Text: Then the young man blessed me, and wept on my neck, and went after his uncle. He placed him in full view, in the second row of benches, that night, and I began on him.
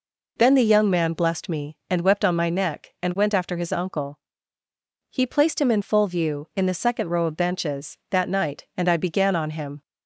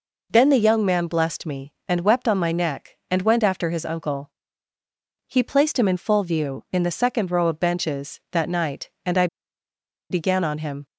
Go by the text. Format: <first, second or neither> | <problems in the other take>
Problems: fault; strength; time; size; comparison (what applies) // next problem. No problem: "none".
first | pauses between "I" and "began"; noticeable; at 9.2 s; 0.84 s long